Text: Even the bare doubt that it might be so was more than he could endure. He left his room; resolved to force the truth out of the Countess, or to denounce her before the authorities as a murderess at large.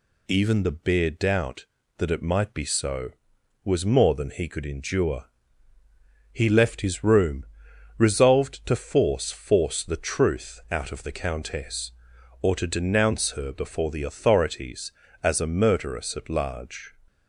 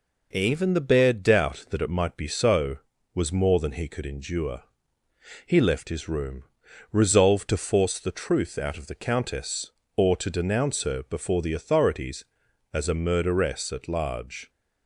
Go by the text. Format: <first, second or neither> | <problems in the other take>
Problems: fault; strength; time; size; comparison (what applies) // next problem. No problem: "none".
second | says "force" twice; at 9.3 s